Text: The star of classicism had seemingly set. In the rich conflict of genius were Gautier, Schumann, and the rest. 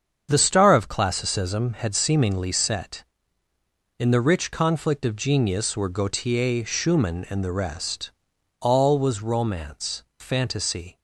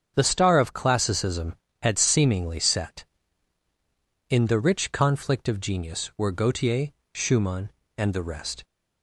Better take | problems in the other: second | starts louder than the rest; strong; until 1.3 s; 7.5 dB; strong in the second // goes on to say "All was romance fantasy"; strong; from 8.6 s on; 2.3 s long

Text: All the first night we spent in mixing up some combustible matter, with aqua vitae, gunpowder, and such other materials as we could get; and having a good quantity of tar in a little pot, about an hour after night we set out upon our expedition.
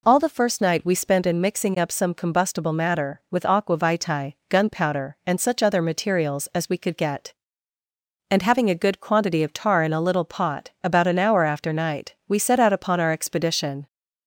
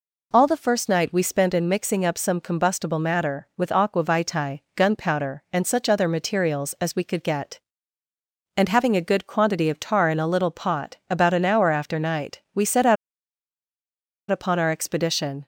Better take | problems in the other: first | pauses between "out" and "upon"; strong; at 12.9 s; 1.3 s long

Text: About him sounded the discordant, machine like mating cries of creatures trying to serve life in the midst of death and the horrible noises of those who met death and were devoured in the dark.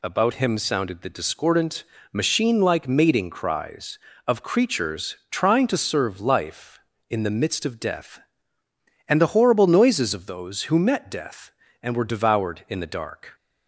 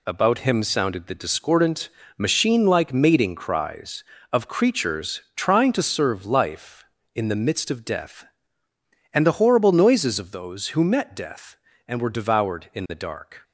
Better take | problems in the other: first | gets quieter; throughout; 6.5 dB

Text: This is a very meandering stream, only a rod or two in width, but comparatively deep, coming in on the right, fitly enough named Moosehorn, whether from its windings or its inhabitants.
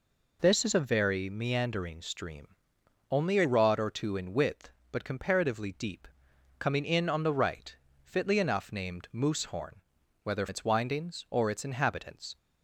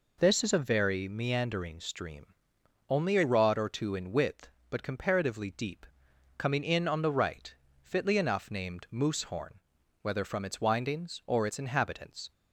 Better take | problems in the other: second | skips "from"; at 10.4 s

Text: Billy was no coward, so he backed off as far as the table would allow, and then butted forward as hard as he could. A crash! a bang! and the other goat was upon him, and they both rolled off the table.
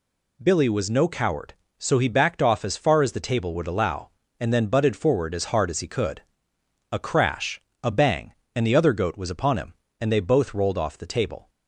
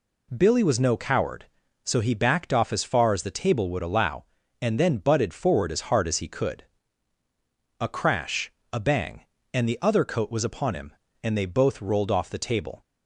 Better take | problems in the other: first | says "coat" for "goat"; at 10.0 s

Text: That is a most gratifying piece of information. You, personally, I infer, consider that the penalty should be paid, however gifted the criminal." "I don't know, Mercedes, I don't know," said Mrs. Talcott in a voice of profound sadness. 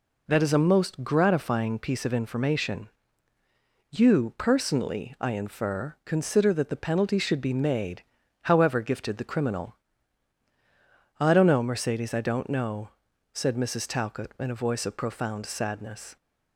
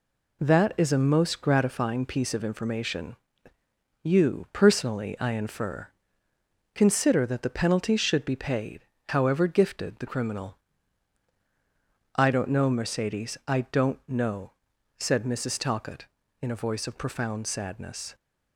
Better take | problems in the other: second | says "made" for "paid"; at 7.5 s

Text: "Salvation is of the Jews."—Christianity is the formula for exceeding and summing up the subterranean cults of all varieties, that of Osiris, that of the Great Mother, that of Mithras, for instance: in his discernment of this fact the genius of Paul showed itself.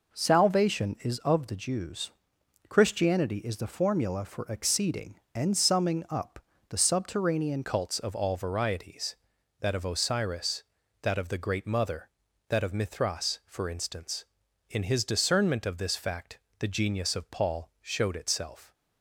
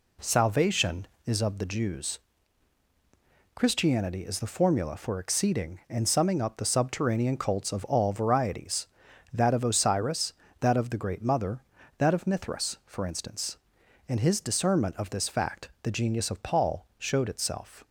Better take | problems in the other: second | pauses between "up" and "the"; slight; at 6.4 s; 0.26 s long // changes voice at "cults"; from 7.6 s on; 11.1 s long // pauses between "fact" and "the"; slight; at 16.3 s; 0.20 s long

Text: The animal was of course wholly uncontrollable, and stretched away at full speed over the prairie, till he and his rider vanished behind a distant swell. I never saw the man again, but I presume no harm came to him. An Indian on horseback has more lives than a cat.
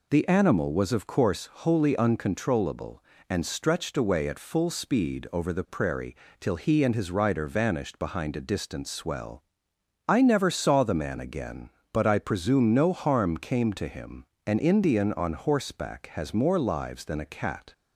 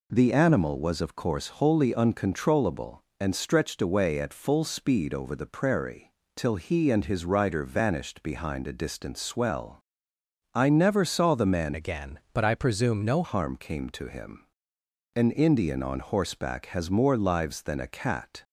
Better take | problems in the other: first | changes voice from "again" to "no"; from 11.7 to 13.2 s; 1.5 s long

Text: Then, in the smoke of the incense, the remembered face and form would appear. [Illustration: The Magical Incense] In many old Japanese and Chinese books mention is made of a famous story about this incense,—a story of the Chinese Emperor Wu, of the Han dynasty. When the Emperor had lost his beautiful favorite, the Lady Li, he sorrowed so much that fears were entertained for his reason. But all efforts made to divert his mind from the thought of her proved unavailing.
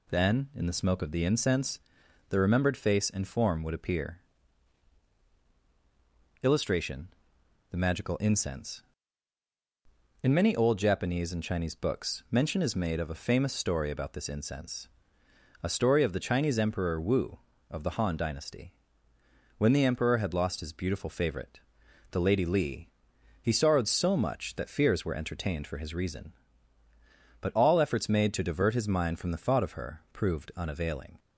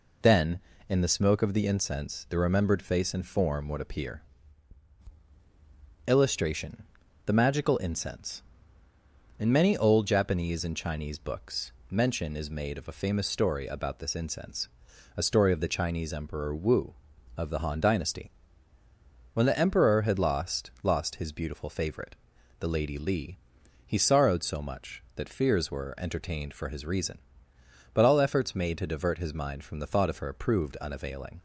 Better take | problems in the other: first | pauses between "books" and "mention"; slight; at 11.7 s; 0.18 s long // says "lost" twice; at 20.8 s

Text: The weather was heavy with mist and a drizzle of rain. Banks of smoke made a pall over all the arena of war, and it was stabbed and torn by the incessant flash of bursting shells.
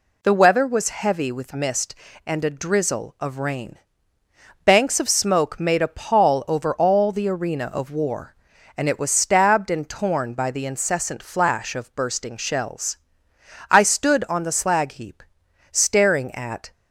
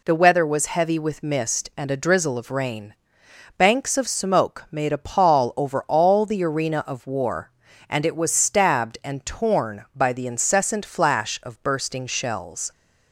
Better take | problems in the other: second | goes on to say "I stood on the slag heap staring at"; strong; from 13.7 s on; 3.0 s long

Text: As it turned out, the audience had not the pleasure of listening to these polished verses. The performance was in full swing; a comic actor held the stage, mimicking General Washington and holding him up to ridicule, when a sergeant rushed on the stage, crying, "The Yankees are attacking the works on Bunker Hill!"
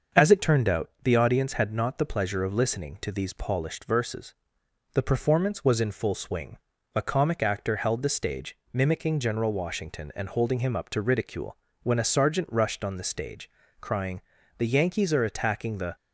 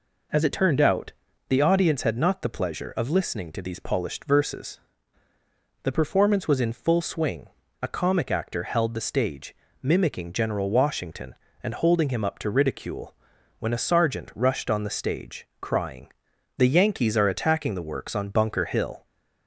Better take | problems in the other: second | starts louder than the rest; until 1.2 s; 6.5 dB // stops before "works on Bunker Hill"; at 15.9 s

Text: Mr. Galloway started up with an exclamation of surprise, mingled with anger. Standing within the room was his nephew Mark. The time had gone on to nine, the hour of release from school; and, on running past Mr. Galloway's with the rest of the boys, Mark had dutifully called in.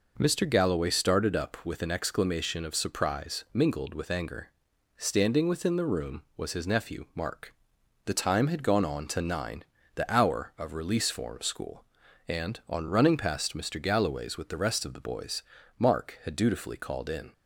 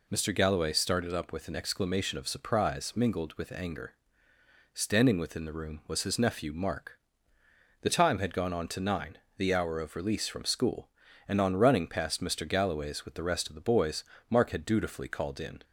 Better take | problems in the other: second | says "form" for "from"; at 11.1 s

